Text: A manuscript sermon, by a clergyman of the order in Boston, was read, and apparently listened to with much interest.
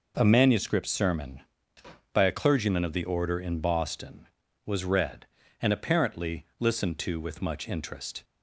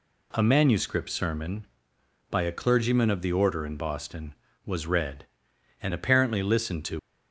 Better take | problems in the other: first | stops before "with much interest"; at 6.9 s

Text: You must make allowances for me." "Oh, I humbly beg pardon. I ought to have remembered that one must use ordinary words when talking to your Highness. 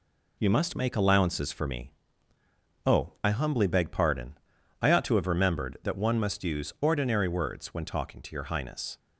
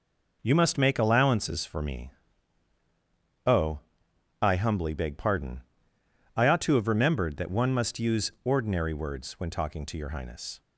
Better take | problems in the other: neither | none

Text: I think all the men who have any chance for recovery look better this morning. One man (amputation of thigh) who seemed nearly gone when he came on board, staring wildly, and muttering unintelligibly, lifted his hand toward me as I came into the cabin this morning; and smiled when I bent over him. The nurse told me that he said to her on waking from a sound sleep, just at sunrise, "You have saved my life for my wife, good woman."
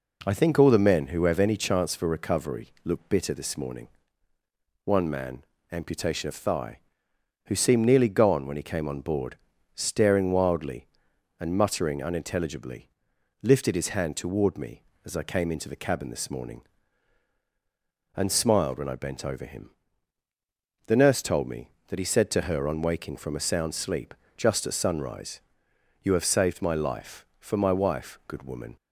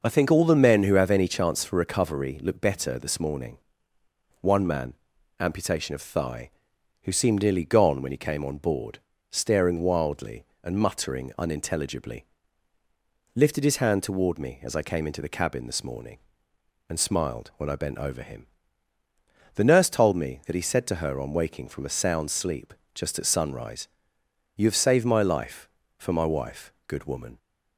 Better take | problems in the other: second | says "bitter" for "better"; at 3.0 s

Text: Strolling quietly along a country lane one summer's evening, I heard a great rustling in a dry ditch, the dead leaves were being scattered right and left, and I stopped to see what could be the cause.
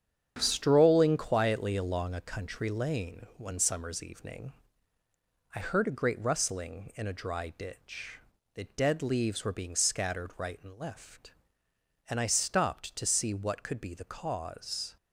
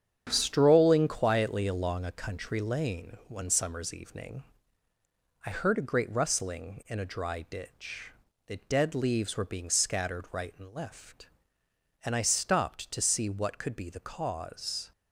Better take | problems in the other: neither | starts louder than the rest; strong; the same in both

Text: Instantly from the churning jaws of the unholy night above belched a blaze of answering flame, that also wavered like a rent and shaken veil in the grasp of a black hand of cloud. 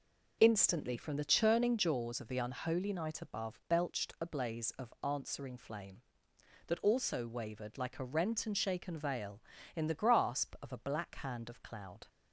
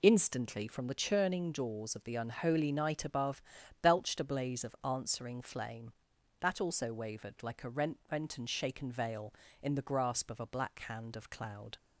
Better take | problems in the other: first | pauses between "above" and "belched"; at 3.4 s; 0.40 s long // says "rent" twice; at 8.1 s

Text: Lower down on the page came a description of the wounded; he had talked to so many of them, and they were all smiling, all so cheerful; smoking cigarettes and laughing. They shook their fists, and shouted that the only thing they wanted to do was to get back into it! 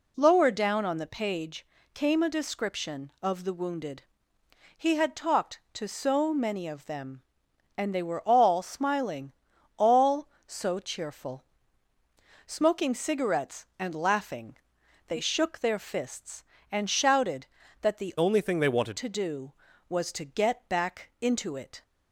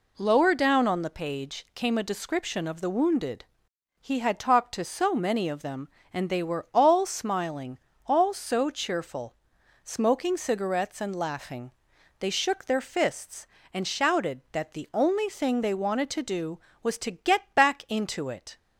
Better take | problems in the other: second | pauses between "page" and "came"; slight; at 1.6 s; 0.26 s long // changes voice from "only" to "wanted"; from 18.1 to 18.9 s; 0.8 s long

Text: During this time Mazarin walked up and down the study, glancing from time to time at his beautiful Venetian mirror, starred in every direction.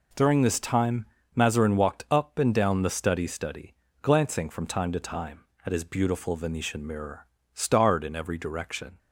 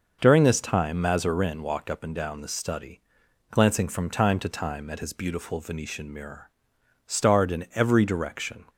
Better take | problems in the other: second | pauses between "time" and "Mazarin"; slight; at 1.0 s; 0.28 s long // says "study" twice; at 3.2 s

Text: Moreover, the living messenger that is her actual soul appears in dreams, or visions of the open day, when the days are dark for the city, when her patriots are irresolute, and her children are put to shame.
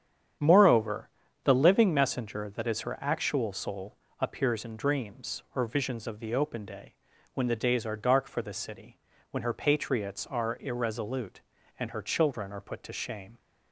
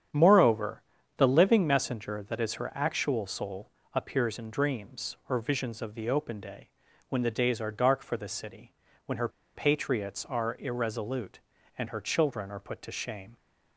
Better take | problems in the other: first | starts louder than the rest; strong; until 1.4 s; 8.5 dB; strong in the first // pauses between "soul" and "appears"; slight; at 3.6 s; 0.24 s long; slight in the first // pauses between "her" and "patriots"; slight; at 9.2 s; 0.26 s long

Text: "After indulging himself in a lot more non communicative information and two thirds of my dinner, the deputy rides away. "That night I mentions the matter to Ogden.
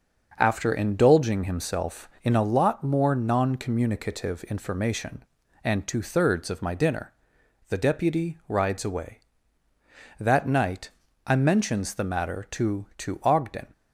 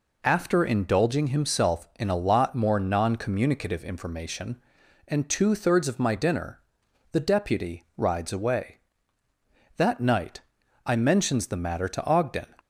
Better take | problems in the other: second | starts louder than the rest; until 1.3 s; 6 dB // pauses between "night" and "I"; slight; at 10.9 s; 0.36 s long; also in the second // says "to" twice; at 12.9 s

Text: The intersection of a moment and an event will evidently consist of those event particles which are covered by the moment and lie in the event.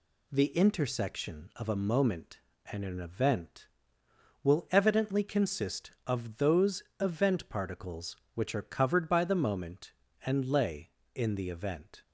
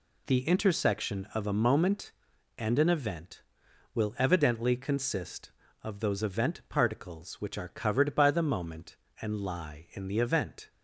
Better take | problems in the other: second | pauses between "those" and "event"; slight; at 6.8 s; 0.18 s long // says "lay" for "lie"; at 10.4 s

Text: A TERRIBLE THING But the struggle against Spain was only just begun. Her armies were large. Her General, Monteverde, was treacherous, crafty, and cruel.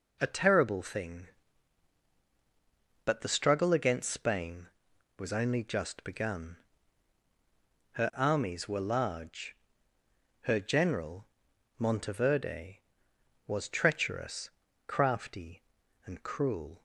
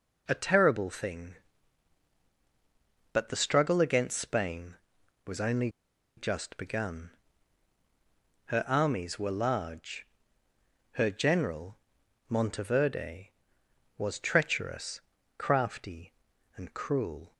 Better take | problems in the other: first | pauses between "only" and "just"; noticeable; at 5.6 s; 0.48 s long

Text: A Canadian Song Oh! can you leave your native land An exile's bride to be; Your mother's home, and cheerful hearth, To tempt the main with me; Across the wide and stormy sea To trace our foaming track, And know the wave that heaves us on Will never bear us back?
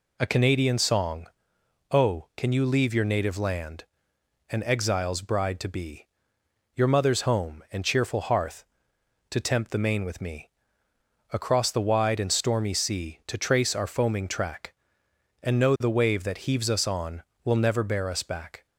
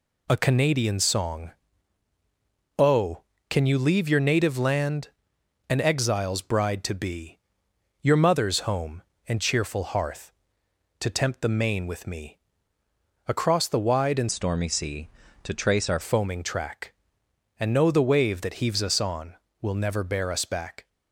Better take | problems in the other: first | pauses between "Song" and "Oh"; strong; at 1.5 s; 1.2 s long; noticeable in the first // pauses between "land" and "An"; noticeable; at 5.0 s; 0.60 s long; noticeable in the first // changes voice from "stormy" to "our"; from 14.2 to 15.9 s; 1.7 s long

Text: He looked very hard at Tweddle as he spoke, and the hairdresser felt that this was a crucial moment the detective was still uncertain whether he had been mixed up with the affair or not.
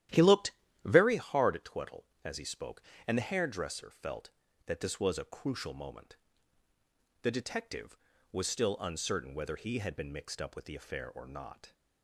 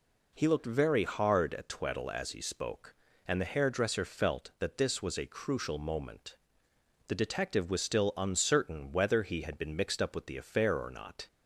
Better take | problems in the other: second | starts louder than the rest; strong; until 1.1 s; 12 dB // pauses between "looked" and "very"; slight; at 0.5 s; 0.34 s long // pauses between "moment" and "the"; at 6.1 s; 1.0 s long; noticeable in the second

